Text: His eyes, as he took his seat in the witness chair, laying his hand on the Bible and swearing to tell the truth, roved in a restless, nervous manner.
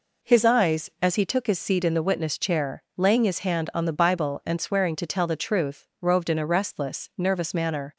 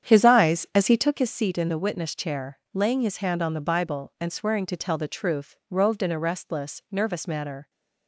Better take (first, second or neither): first